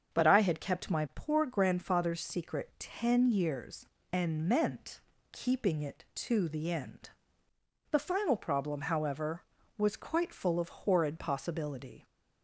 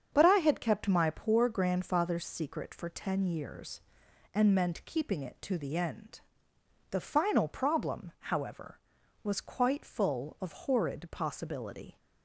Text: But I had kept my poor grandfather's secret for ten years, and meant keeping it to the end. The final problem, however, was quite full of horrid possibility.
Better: second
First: starts louder than the rest; until 1.1 s; 7 dB // skips "for"; at 2.7 s // pauses between "meant" and "keeping"; slight; at 5.0 s; 0.32 s long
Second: starts louder than the rest; until 1.1 s; 7 dB

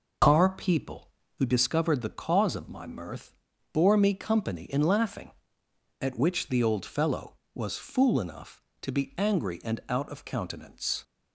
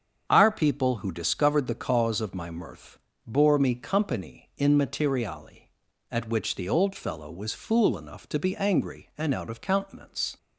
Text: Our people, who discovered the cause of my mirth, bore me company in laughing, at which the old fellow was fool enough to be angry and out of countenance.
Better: first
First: none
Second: starts louder than the rest; strong; until 1.2 s; 7.5 dB // says "materiali" for "laughing"; at 4.7 s

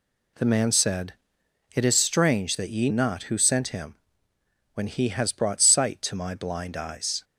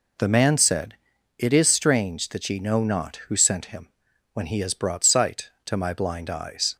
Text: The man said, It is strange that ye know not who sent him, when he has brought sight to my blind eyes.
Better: second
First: skips "know"; at 2.8 s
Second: none

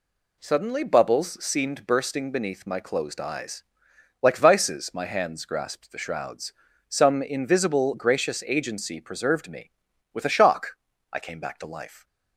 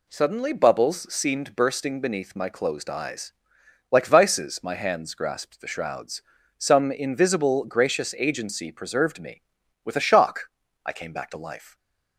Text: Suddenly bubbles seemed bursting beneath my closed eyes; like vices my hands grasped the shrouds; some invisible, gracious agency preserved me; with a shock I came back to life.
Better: neither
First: pauses between "shock" and "I"; slight; at 10.7 s; 0.34 s long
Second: pauses between "shock" and "I"; slight; at 10.4 s; 0.34 s long

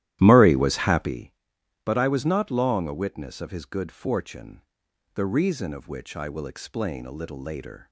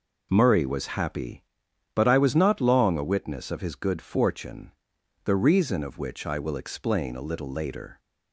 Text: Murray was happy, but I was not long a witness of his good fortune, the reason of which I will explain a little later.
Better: second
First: starts louder than the rest; strong; until 1.2 s; 13.5 dB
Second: none

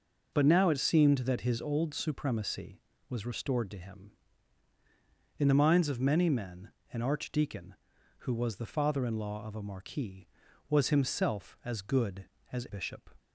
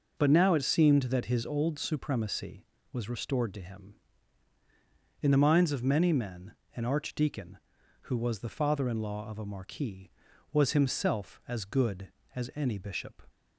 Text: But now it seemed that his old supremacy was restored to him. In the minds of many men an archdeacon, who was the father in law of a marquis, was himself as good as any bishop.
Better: second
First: pauses between "men" and "an"; slight; at 6.6 s; 0.22 s long // skips "any"; at 12.6 s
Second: pauses between "men" and "an"; slight; at 6.5 s; 0.22 s long

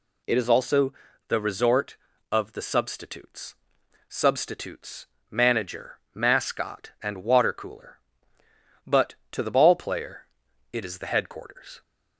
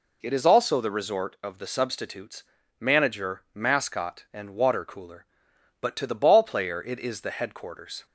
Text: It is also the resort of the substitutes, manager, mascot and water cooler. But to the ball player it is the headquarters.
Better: second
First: pauses between "also" and "the"; slight; at 0.9 s; 0.34 s long // says "substitutes" twice; at 4.0 s // pauses between "player" and "it"; at 10.2 s; 0.44 s long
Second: none

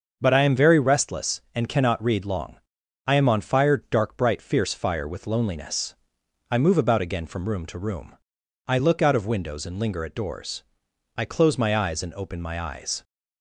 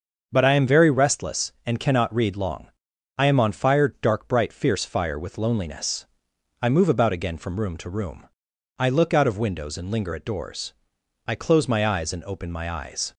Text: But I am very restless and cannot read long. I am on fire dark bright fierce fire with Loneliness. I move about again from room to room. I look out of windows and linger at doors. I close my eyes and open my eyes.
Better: neither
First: starts louder than the rest; until 1.2 s; 6.5 dB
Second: starts louder than the rest; until 1.3 s; 6.5 dB

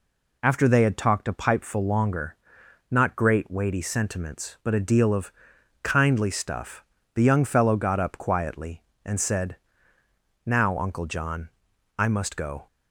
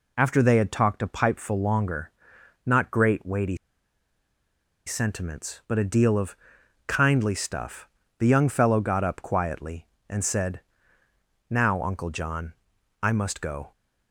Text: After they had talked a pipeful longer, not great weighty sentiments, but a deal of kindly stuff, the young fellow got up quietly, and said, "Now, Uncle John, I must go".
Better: first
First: pauses between "of" and "kindly"; noticeable; at 5.3 s; 0.52 s long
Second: pauses between "weighty" and "sentiments"; strong; at 3.5 s; 1.3 s long // pauses between "of" and "kindly"; noticeable; at 6.3 s; 0.52 s long

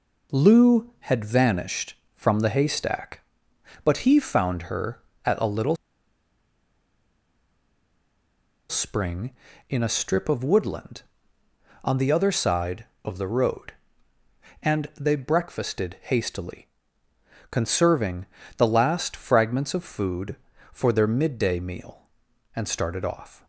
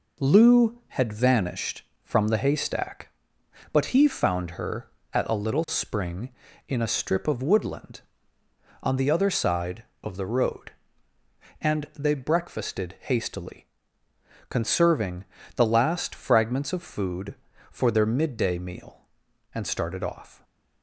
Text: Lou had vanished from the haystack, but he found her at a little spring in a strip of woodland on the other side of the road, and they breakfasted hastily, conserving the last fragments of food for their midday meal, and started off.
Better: second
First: pauses between "little" and "spring"; strong; at 5.7 s; 2.9 s long // pauses between "conserving" and "the"; slight; at 18.2 s; 0.32 s long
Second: pauses between "conserving" and "the"; slight; at 15.2 s; 0.32 s long

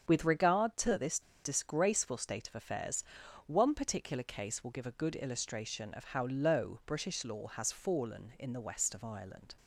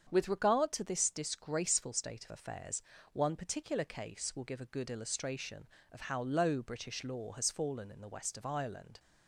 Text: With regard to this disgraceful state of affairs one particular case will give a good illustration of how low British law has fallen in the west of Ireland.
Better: second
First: starts louder than the rest; strong; until 1.1 s; 7.5 dB // pauses between "this" and "disgraceful"; slight; at 1.2 s; 0.23 s long // pauses between "affairs" and "one"; at 3.0 s; 0.44 s long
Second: starts louder than the rest; strong; until 1.1 s; 7.5 dB // pauses between "affairs" and "one"; slight; at 2.7 s; 0.32 s long

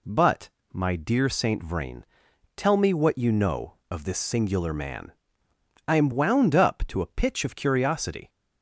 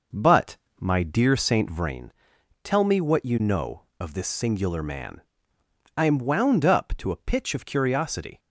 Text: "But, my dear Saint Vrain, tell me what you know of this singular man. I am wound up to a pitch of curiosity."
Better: first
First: none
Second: starts louder than the rest; noticeable; until 2.0 s; 5.5 dB

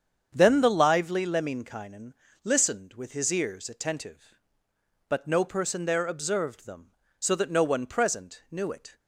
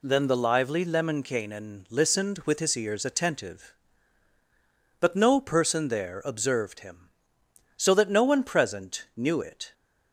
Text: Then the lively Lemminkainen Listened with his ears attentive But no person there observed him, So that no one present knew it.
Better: second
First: starts louder than the rest; strong; until 1.3 s; 7.5 dB // pauses between "Lemminkainen" and "Listened"; slight; at 2.1 s; 0.30 s long // says "them" for "him"; at 6.6 s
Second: none

